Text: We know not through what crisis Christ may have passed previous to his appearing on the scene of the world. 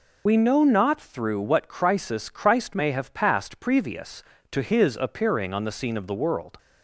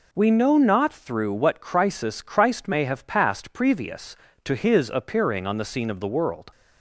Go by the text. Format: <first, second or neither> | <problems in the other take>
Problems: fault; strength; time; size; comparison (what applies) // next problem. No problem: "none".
second | loses the start of "We"; at 0.2 s; 60 ms